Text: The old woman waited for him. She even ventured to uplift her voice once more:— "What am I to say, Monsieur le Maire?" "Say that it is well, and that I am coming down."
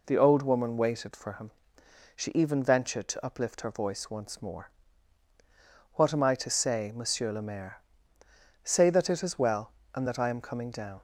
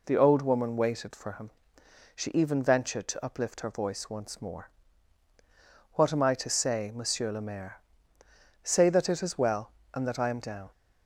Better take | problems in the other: first | skips "coming"; at 10.4 s

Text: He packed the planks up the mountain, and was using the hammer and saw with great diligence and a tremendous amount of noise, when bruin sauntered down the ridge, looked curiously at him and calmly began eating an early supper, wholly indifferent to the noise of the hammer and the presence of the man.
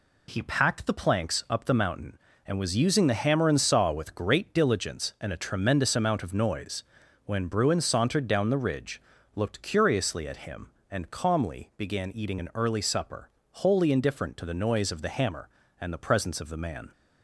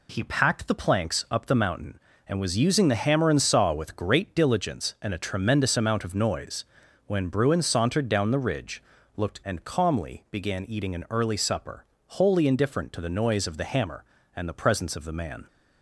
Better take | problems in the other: first | skips "curiously at him"; at 9.4 s

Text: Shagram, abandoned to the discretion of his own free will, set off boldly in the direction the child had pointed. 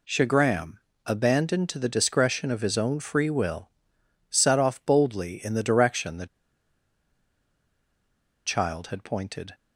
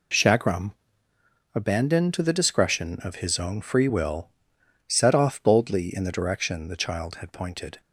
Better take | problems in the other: second | pauses between "the" and "child"; strong; at 6.2 s; 2.2 s long

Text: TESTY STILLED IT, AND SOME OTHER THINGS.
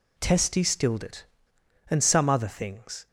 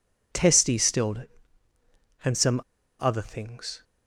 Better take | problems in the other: first | pauses between "SOME" and "OTHER"; at 2.6 s; 0.37 s long

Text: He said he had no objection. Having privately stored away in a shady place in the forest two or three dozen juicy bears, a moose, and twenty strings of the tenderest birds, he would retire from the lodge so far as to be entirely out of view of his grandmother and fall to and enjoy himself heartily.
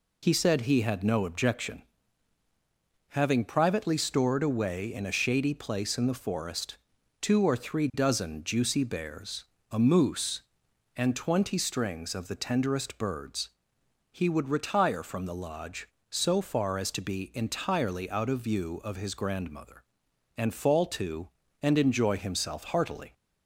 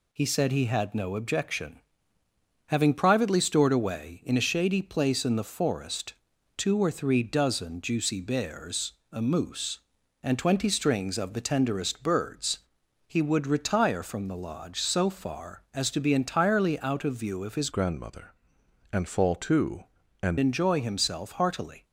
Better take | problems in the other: first | pauses between "forest" and "two"; at 6.1 s; 0.44 s long; also in the first // changes voice from "grandmother" to "and"; from 17.7 to 20.3 s; 2.6 s long

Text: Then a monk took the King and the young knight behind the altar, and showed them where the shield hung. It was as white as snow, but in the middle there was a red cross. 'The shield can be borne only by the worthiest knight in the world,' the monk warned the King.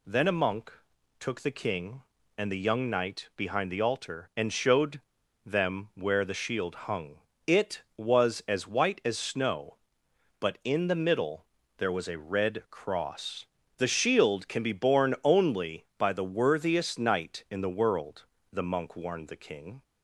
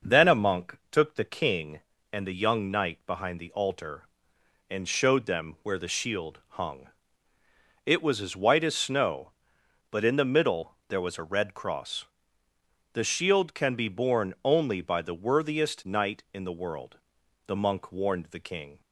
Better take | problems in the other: second | pauses between "monk" and "took"; noticeable; at 0.7 s; 0.48 s long; slight in the second // pauses between "showed" and "them"; at 4.9 s; 0.45 s long // pauses between "middle" and "there"; slight; at 11.4 s; 0.32 s long

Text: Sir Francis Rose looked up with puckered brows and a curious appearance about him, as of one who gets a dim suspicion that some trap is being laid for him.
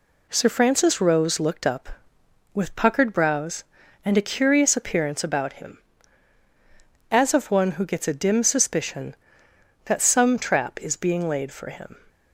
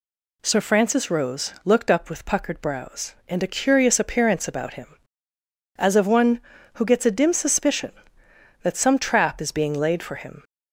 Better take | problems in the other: neither | none

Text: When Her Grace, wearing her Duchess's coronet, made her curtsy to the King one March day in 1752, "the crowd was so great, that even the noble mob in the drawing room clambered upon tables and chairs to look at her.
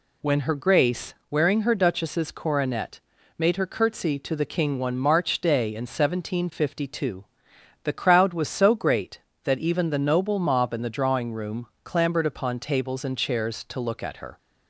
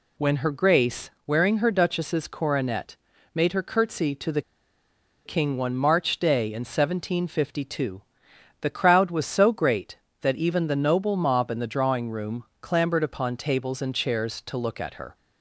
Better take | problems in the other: first | pauses between "the" and "King"; noticeable; at 4.4 s; 0.84 s long // pauses between "room" and "clambered"; slight; at 12.4 s; 0.18 s long; slight in the first

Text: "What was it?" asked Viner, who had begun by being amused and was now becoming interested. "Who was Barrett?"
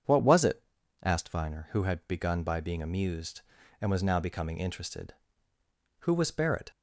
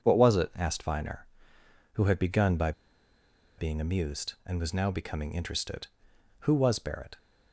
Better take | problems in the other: first | pauses between "by" and "being"; noticeable; at 2.7 s; 0.86 s long

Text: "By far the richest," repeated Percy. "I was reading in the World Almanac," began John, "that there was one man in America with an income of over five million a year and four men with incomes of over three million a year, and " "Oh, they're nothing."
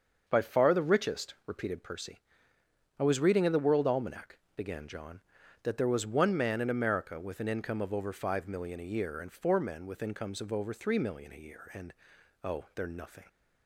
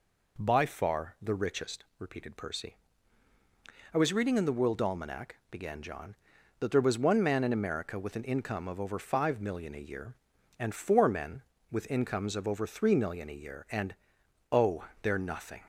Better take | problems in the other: second | starts louder than the rest; until 1.8 s; 6.5 dB

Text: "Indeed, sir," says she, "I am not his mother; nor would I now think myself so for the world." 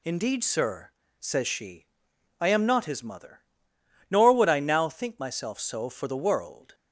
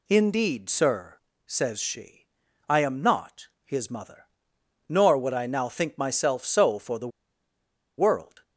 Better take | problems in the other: first | pauses between "not" and "his"; slight; at 3.4 s; 0.16 s long // pauses between "the" and "world"; noticeable; at 7.0 s; 0.90 s long

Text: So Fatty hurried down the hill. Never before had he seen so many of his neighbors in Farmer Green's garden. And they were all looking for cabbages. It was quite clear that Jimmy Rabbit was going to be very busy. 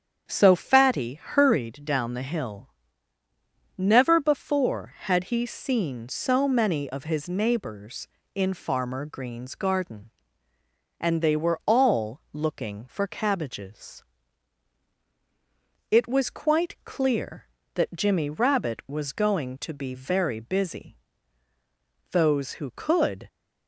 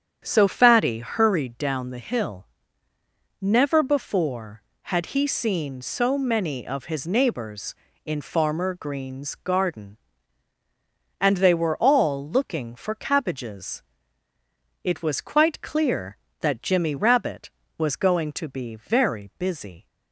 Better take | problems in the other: second | starts louder than the rest; strong; until 1.2 s; 8 dB; strong in the second // goes on to say "Those who could"; noticeable; from 22.1 s on; 1.1 s long

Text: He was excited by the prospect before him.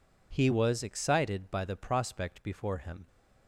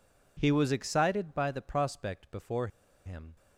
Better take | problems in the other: first | pauses between "before" and "him"; at 2.6 s; 0.37 s long

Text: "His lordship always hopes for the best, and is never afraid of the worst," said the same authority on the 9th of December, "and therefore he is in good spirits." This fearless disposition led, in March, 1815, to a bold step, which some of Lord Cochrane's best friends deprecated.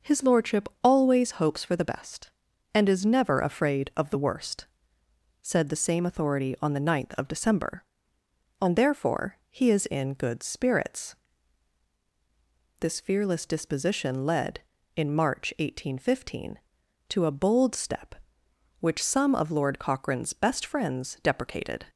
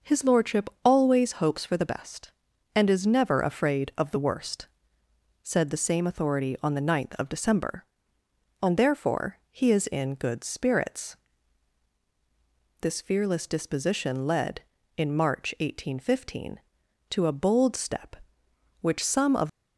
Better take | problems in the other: first | pauses between "lordship" and "always"; slight; at 0.6 s; 0.16 s long; slight in the first // stops before "Lord Cochrane's best friends deprecated"; at 19.4 s

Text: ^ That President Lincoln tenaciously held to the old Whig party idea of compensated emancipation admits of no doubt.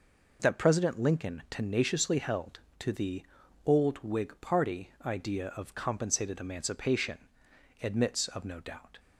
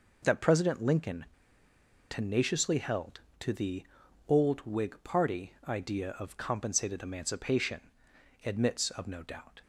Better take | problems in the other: first | pauses between "Lincoln" and "tenaciously"; noticeable; at 1.2 s; 0.85 s long // pauses between "the" and "old"; at 3.8 s; 0.42 s long; also in the first // pauses between "emancipation" and "admits"; noticeable; at 7.7 s; 0.64 s long; noticeable in the first

